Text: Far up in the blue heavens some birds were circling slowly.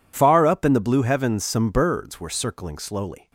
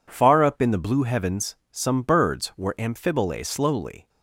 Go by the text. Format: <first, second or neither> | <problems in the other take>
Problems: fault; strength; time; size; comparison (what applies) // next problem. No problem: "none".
first | pauses between "heavens" and "some"; slight; at 1.5 s; 0.16 s long // says "amphibole" for "circling"; at 2.7 s